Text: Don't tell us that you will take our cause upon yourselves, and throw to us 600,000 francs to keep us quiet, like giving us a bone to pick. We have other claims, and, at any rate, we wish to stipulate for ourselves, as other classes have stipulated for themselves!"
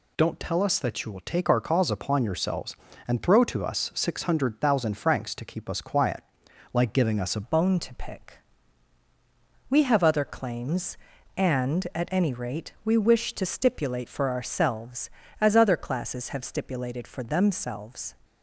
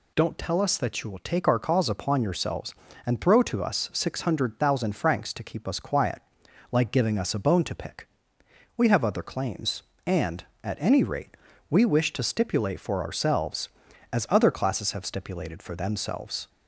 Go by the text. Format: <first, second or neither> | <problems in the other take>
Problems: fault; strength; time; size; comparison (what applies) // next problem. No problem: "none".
second | changes voice at "bone"; from 7.4 s on; 10.7 s long